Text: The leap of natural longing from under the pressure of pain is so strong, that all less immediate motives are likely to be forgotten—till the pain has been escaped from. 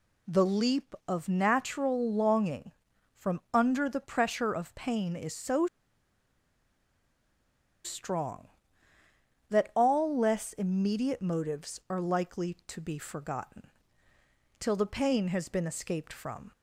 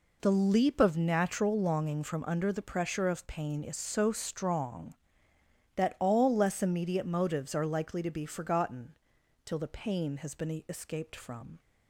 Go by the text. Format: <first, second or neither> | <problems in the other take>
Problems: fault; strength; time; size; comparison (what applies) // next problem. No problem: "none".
second | pauses between "so" and "strong"; strong; at 5.6 s; 2.1 s long